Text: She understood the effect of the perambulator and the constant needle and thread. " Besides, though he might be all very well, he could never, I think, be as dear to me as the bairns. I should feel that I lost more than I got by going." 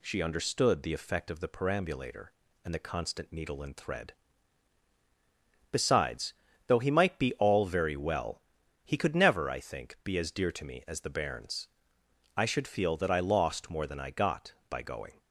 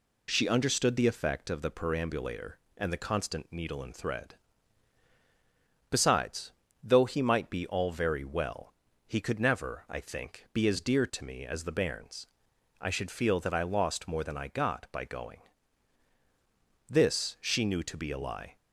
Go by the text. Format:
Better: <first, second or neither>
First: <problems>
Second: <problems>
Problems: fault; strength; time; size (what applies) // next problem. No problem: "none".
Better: first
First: none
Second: goes on to say "This she knew to be a lie"; strong; from 16.8 s on; 1.6 s long